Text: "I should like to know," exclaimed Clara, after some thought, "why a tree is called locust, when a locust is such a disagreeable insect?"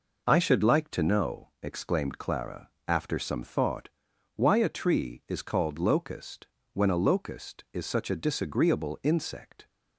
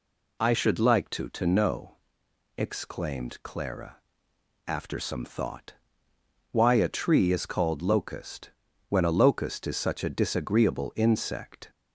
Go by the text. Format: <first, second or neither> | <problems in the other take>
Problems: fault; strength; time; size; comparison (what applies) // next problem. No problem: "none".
first | says "to" twice; at 1.2 s